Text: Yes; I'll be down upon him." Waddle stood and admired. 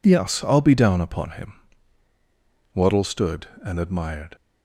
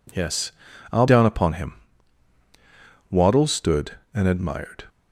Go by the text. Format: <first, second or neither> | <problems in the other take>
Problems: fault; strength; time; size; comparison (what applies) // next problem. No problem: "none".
first | skips "be"; at 1.0 s